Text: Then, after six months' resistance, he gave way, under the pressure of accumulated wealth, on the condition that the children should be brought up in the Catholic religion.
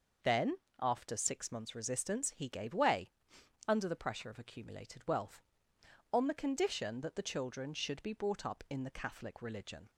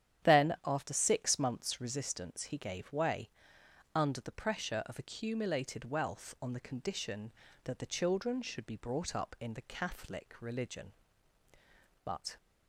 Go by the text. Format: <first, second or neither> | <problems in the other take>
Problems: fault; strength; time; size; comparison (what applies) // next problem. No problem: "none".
first | starts louder than the rest; strong; until 1.3 s; 10.5 dB // goes on to say "But"; slight; from 12.0 s on; 0.34 s long